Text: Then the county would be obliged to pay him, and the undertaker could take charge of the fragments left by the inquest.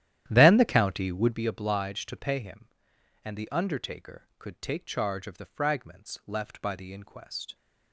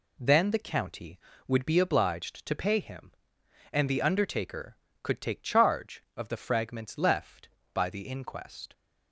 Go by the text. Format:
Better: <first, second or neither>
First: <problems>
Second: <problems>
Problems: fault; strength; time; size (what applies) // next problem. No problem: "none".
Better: second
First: starts louder than the rest; strong; until 1.4 s; 12 dB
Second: none